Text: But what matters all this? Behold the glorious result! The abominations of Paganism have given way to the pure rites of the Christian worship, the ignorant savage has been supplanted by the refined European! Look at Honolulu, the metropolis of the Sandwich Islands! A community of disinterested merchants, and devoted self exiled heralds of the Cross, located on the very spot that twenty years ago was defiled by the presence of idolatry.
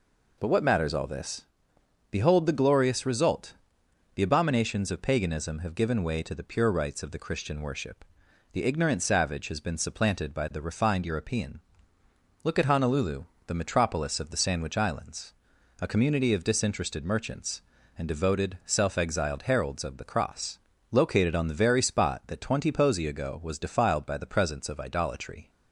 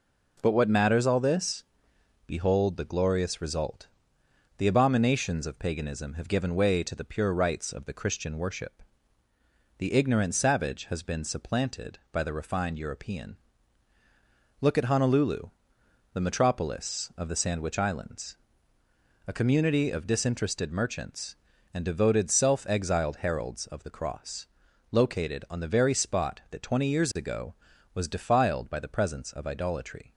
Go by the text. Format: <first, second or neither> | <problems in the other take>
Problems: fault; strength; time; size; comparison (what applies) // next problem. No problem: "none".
second | says "posy" for "years"; at 22.7 s